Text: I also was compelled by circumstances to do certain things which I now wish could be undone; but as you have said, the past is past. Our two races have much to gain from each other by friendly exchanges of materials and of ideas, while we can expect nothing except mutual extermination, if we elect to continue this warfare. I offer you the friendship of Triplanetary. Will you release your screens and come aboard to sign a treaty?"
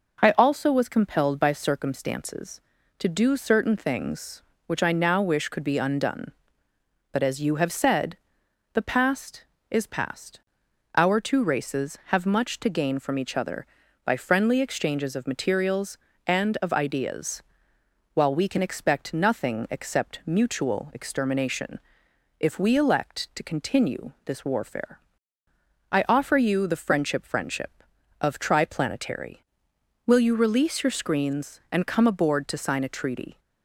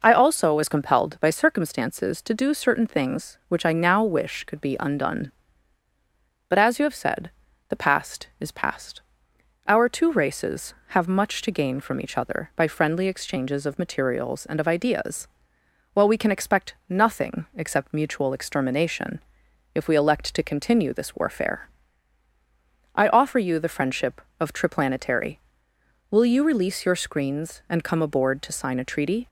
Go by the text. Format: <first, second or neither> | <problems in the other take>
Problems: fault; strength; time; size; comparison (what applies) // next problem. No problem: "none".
second | says "friendship" twice; at 27.2 s